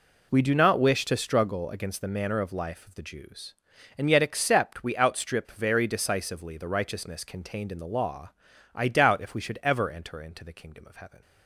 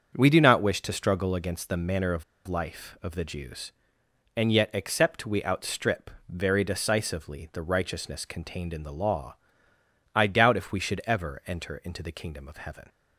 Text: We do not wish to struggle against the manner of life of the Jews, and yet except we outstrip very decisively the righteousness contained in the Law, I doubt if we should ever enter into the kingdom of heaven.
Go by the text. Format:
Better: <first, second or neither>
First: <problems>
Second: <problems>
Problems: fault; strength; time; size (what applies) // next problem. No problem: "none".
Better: first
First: none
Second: starts louder than the rest; until 1.1 s; 7 dB // pauses between "of" and "life"; slight; at 2.2 s; 0.24 s long // pauses between "outstrip" and "very"; slight; at 6.1 s; 0.18 s long